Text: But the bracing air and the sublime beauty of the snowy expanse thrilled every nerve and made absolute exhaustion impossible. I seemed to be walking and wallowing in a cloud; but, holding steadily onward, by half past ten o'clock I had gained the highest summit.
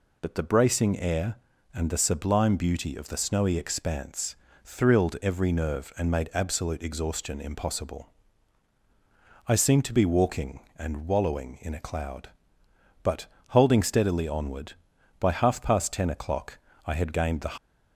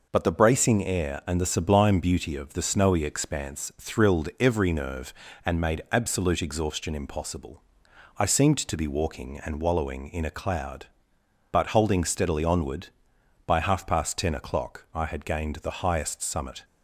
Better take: second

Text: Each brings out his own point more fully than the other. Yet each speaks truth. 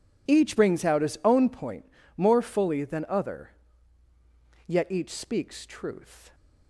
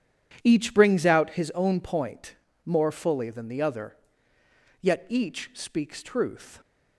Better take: second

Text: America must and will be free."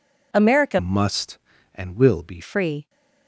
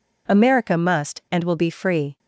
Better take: second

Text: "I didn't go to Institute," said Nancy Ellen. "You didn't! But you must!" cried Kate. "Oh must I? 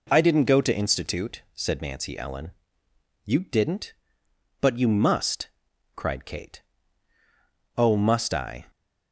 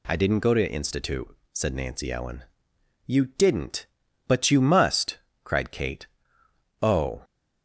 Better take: first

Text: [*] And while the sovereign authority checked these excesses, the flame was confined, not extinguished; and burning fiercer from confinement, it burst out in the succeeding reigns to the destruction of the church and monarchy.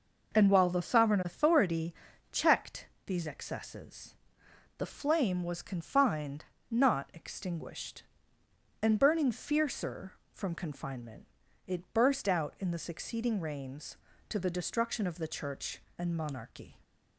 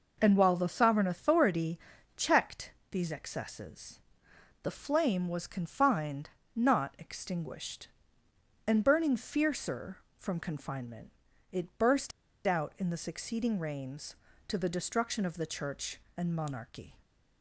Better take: first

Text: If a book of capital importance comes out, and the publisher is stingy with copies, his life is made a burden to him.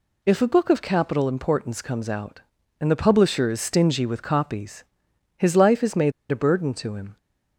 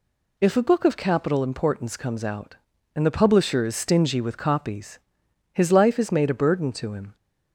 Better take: second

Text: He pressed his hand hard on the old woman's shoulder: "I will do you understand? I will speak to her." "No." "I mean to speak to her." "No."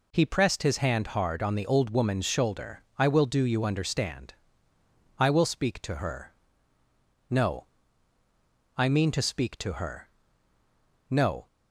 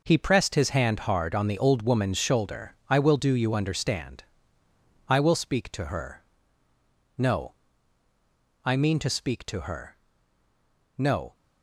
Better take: first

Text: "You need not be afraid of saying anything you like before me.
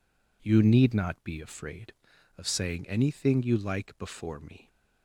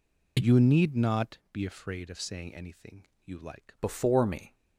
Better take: first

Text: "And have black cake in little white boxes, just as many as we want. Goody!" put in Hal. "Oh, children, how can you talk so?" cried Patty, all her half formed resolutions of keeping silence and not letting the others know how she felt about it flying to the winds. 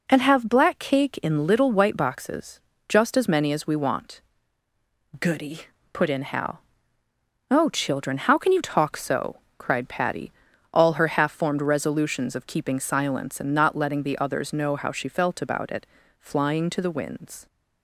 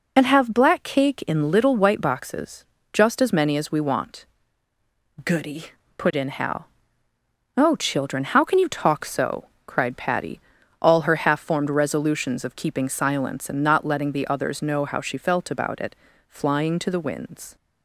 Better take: first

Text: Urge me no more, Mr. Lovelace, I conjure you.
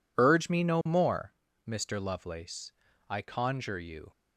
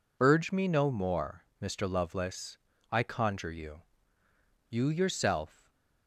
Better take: first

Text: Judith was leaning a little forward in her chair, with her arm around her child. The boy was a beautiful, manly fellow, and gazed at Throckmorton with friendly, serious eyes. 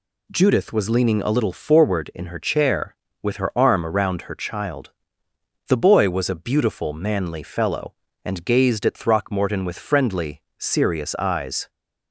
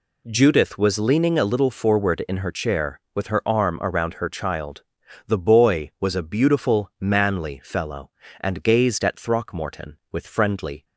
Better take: first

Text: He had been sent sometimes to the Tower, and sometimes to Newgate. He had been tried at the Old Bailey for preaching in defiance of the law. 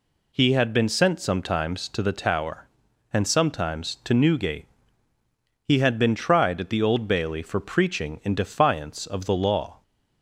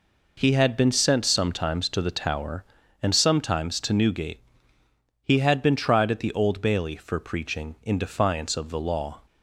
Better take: neither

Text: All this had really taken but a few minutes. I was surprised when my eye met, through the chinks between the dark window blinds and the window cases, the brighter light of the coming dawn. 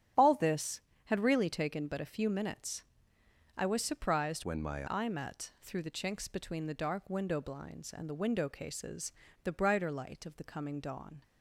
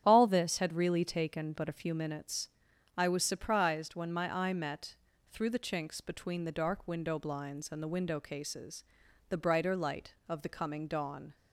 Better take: second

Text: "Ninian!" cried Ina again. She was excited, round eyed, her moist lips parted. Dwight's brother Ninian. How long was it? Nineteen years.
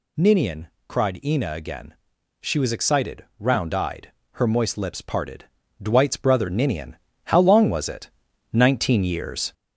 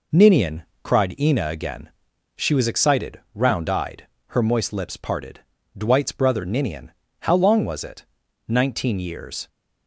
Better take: second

